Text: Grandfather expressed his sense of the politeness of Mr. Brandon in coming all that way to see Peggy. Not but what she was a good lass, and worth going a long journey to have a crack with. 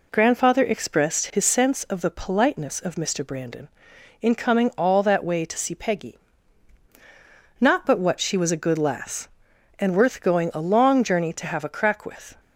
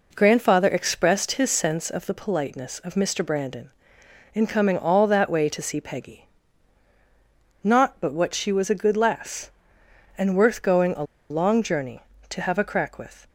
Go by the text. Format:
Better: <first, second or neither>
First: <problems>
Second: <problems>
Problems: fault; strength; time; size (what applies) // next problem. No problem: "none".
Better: first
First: none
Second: pauses between "a" and "long"; slight; at 11.0 s; 0.26 s long